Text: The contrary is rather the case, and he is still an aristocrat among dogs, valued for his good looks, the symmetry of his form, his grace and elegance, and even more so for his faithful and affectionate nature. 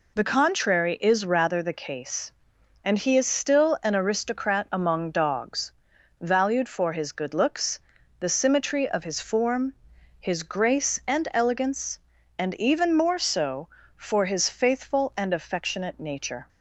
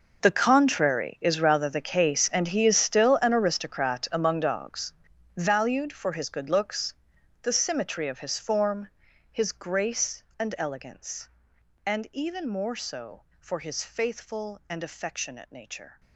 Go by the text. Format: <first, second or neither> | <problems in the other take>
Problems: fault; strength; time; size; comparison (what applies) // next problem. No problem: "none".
first | gets quieter; strong; throughout; 16.5 dB